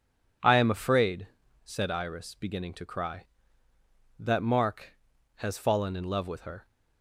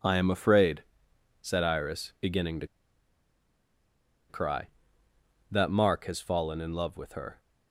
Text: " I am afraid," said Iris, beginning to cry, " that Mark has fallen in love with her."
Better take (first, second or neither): first